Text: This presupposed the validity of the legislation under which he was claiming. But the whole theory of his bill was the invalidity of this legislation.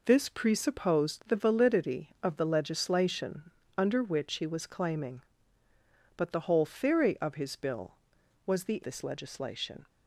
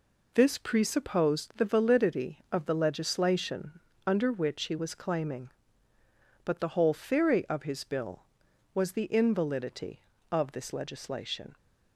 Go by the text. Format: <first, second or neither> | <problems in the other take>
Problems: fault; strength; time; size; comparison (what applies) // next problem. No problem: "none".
second | pauses between "legislation" and "under"; slight; at 3.5 s; 0.26 s long; slight in the second // skips "invalidity of"; at 8.8 s